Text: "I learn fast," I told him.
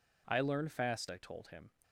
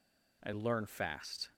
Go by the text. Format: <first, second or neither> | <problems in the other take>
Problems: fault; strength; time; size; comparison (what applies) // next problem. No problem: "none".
first | stops before "I told him"; at 1.5 s